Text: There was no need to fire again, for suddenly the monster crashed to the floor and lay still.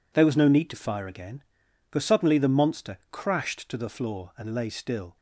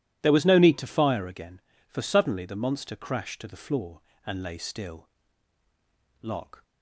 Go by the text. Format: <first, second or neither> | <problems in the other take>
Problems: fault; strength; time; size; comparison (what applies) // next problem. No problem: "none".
first | goes on to say "Locke"; slight; from 6.2 s on; 0.40 s long